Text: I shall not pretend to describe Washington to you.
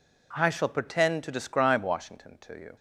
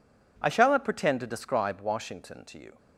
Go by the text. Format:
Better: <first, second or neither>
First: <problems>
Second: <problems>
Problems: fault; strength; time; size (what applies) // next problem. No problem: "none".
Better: second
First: skips "not"; at 0.6 s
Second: none